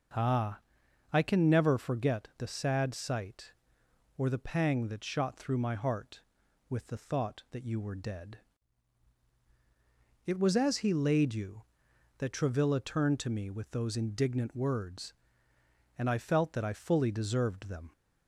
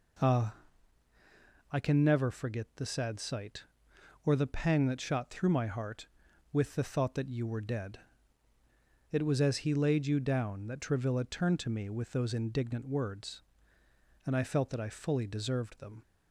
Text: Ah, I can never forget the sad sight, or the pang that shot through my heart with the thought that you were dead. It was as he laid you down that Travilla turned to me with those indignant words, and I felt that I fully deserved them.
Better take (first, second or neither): second